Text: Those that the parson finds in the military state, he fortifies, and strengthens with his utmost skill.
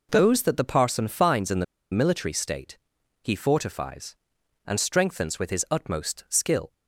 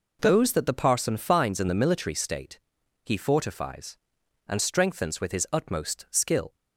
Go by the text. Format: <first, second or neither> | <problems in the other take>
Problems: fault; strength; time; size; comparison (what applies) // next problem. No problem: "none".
second | pauses between "the" and "military"; slight; at 1.6 s; 0.29 s long